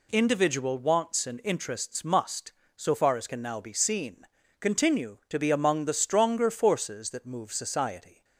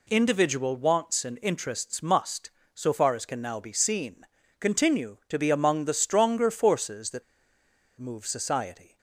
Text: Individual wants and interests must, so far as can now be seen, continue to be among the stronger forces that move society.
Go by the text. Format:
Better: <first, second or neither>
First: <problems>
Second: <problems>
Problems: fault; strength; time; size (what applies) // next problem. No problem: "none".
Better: first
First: none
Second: pauses between "that" and "move"; noticeable; at 7.2 s; 0.76 s long